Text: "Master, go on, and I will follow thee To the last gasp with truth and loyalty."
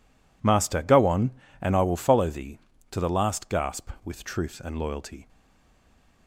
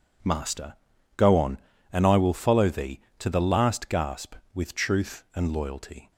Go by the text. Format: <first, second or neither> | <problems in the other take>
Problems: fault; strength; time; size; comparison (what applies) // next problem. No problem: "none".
second | stays silent after the last word; slight; from 5.2 s on; 1.0 s long